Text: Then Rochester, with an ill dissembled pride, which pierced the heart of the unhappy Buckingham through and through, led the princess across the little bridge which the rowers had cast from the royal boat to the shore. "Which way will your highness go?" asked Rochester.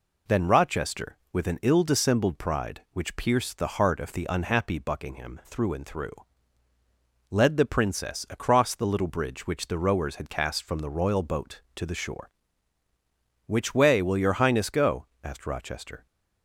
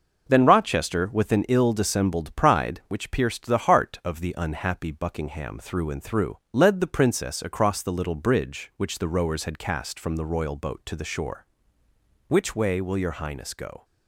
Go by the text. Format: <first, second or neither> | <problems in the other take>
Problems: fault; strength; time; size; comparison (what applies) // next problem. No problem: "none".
first | stops before "asked Rochester"; at 13.8 s